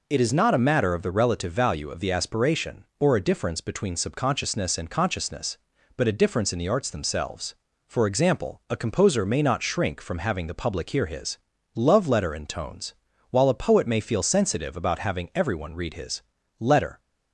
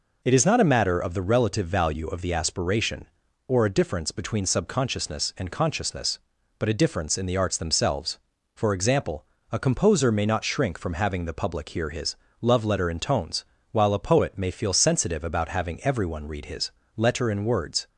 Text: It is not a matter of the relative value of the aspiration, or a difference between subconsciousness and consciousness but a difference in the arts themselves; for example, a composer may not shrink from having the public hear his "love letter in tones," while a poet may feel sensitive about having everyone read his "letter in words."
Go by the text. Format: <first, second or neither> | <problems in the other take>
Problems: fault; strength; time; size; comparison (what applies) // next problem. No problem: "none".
second | pauses between "his" and "love"; slight; at 11.3 s; 0.36 s long; slight in the second // pauses between "his" and "letter"; at 16.2 s; 0.38 s long; slight in the second // stops before "in words"; at 16.9 s